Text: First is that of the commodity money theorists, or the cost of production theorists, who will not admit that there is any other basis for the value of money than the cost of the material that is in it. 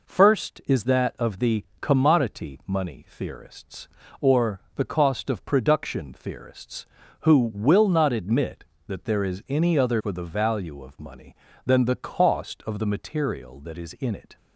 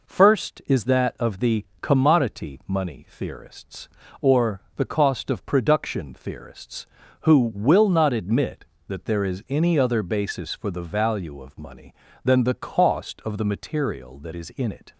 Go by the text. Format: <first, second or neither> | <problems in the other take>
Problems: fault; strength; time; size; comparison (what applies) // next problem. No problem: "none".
second | pauses between "the" and "commodity"; slight; at 1.6 s; 0.16 s long; slight in the second // pauses between "or" and "the"; slight; at 4.6 s; 0.16 s long; slight in the second // skips "basis"; at 9.9 s